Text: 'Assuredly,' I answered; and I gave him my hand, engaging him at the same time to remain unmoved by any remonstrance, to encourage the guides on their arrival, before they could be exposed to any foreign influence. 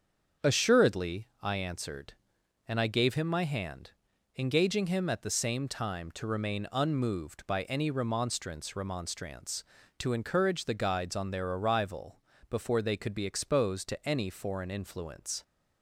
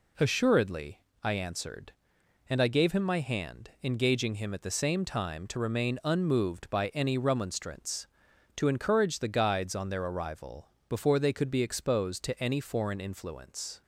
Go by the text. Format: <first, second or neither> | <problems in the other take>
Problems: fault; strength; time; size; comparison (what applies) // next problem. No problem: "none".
second | starts louder than the rest; strong; until 1.5 s; 7.5 dB // says "remonstrance" twice; at 8.7 s